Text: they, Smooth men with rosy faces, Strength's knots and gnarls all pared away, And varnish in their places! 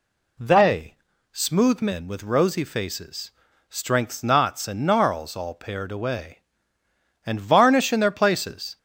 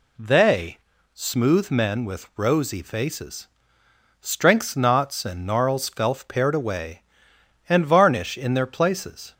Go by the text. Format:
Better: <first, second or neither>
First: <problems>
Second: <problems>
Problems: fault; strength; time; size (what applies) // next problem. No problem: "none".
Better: first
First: none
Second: says "felf" for "all"; at 5.8 s